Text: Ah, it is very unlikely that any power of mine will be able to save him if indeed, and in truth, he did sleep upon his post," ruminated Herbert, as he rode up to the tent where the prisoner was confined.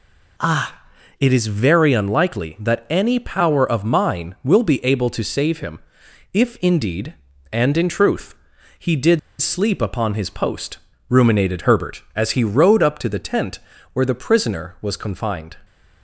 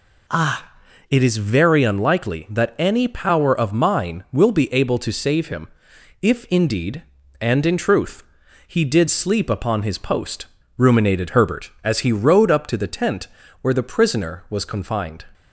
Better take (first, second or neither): second